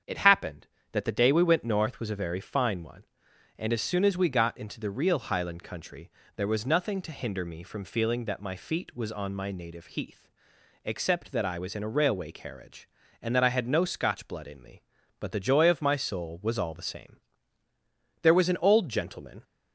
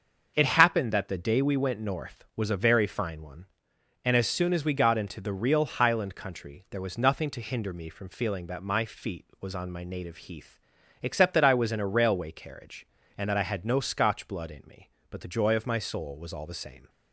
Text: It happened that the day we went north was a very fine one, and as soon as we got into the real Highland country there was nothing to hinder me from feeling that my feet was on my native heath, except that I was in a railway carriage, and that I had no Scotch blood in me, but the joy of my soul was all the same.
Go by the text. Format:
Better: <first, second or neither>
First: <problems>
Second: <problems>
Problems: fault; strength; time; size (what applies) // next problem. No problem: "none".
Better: second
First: starts louder than the rest; strong; until 1.2 s; 7.5 dB // pauses between "country" and "there"; slight; at 6.1 s; 0.24 s long // goes on to say "There was an old gentleman"; noticeable; from 18.2 s on; 1.2 s long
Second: starts louder than the rest; until 1.3 s; 6.5 dB